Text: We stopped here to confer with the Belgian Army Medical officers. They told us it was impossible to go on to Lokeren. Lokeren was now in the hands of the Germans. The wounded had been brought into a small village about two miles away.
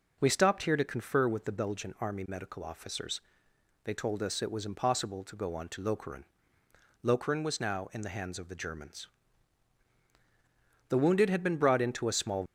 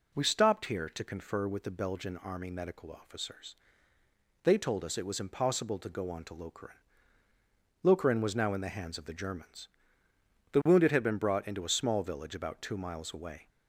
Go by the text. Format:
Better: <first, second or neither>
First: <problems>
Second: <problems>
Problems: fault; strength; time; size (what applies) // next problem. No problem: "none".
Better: second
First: stops before "village about two miles away"; at 12.4 s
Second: none